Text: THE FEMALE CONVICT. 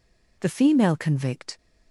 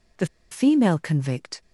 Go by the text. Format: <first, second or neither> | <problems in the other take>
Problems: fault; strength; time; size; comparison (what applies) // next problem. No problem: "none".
first | pauses between "THE" and "FEMALE"; slight; at 0.2 s; 0.23 s long